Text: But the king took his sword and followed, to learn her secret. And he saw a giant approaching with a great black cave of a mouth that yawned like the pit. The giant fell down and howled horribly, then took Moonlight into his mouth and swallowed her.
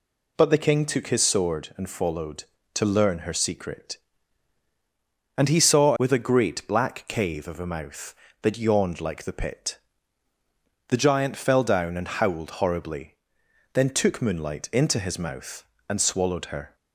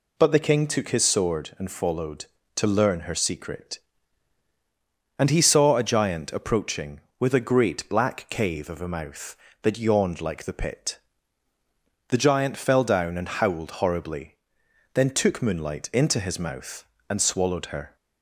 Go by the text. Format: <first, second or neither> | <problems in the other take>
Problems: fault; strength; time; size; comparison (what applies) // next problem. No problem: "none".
second | skips "a giant approaching"; at 5.9 s